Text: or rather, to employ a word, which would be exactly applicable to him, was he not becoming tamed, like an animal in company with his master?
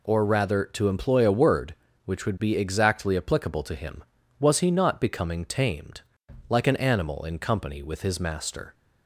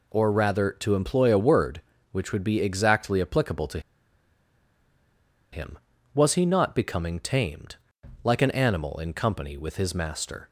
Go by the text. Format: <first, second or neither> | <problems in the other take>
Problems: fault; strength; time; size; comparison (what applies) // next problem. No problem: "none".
first | pauses between "to" and "him"; strong; at 3.7 s; 1.7 s long